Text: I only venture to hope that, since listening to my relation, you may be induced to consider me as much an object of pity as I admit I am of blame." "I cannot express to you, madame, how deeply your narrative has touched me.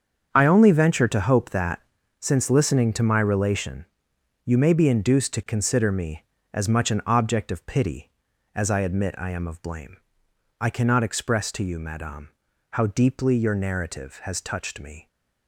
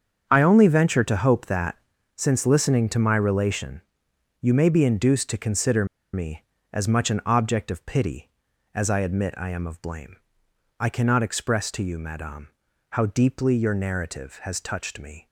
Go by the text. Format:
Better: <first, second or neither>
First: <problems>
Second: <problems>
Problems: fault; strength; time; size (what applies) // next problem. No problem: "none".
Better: first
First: starts louder than the rest; strong; until 1.3 s; 7 dB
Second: starts louder than the rest; strong; until 1.2 s; 7 dB // pauses between "consider" and "me"; slight; at 5.8 s; 0.28 s long